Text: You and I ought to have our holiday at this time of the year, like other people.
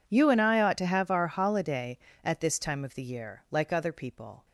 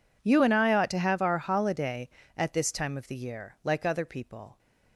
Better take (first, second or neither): neither